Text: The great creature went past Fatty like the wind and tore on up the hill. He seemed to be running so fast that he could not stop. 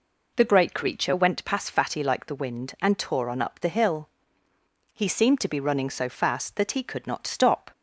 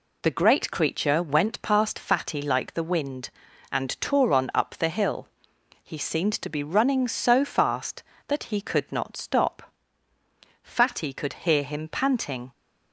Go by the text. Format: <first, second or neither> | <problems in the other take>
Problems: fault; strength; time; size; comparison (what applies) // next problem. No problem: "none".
first | goes on to say "Fatty could hear him panting"; strong; from 10.6 s on; 1.8 s long